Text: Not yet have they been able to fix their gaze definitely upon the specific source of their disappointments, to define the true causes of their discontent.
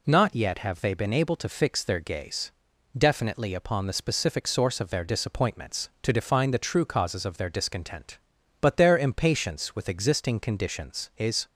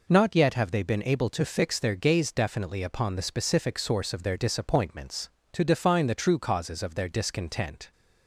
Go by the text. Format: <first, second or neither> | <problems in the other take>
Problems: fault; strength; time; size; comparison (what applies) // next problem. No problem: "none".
second | pauses between "gaze" and "definitely"; at 2.5 s; 0.44 s long // goes on to say "But their impatience with existing conditions is"; strong; from 8.6 s on; 2.8 s long